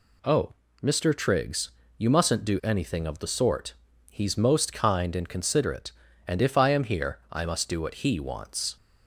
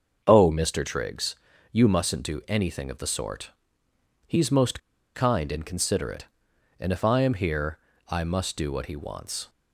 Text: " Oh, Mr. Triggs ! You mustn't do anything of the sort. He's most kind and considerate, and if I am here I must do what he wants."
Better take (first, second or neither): first